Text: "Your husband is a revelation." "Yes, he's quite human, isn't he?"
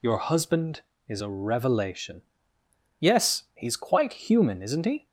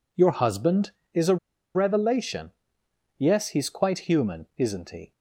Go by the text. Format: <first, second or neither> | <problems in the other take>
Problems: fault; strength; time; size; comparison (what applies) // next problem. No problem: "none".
first | pauses between "a" and "revelation"; at 1.3 s; 0.37 s long